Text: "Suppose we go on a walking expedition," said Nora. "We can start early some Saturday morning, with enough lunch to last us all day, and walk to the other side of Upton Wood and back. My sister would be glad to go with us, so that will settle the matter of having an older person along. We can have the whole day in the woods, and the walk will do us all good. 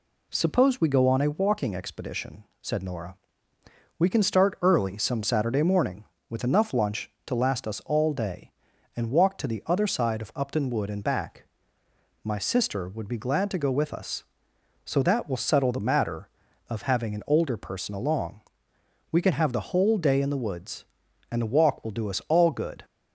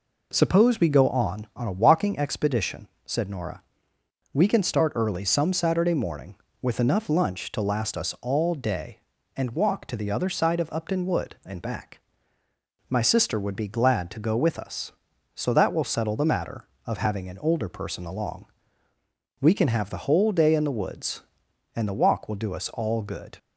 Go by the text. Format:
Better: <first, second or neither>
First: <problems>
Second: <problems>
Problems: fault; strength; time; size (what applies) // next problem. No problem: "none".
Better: first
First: none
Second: says "on" twice; at 1.5 s